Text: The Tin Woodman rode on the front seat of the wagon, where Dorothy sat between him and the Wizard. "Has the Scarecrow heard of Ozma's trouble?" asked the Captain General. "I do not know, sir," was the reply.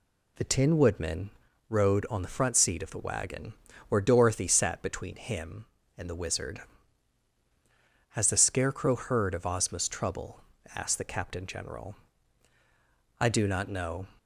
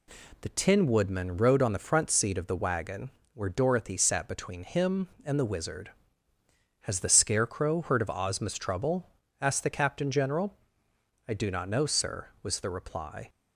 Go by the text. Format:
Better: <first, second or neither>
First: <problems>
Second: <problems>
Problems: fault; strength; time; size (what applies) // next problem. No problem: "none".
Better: second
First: pauses between "Woodman" and "rode"; at 1.3 s; 0.38 s long // stops before "sir was the reply"; at 14.1 s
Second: none